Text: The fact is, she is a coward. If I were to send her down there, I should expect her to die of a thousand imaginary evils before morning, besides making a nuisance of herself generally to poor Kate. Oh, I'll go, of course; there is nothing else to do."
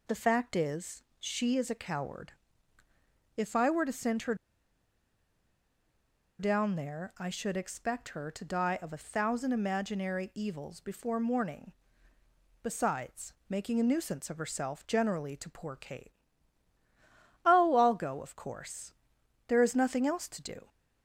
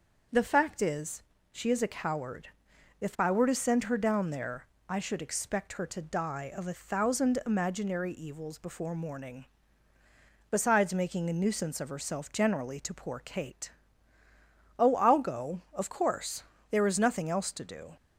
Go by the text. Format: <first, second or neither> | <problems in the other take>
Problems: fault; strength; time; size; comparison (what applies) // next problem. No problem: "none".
second | pauses between "her" and "down"; strong; at 4.3 s; 2.0 s long // pauses between "besides" and "making"; slight; at 13.3 s; 0.16 s long